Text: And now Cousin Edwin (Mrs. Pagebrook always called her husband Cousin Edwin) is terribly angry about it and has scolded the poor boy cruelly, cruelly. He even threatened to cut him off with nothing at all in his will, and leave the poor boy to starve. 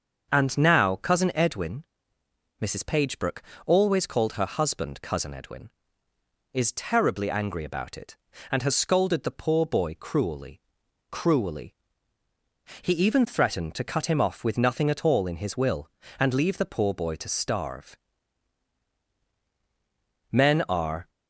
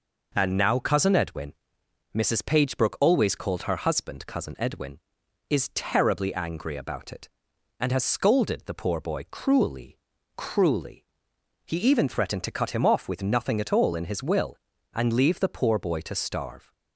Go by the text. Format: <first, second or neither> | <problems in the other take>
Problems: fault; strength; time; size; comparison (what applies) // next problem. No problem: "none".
second | starts louder than the rest; until 1.3 s; 6.5 dB // pauses between "Pagebrook" and "always"; slight; at 3.4 s; 0.24 s long // goes on to say "Men are"; noticeable; from 20.3 s on; 0.78 s long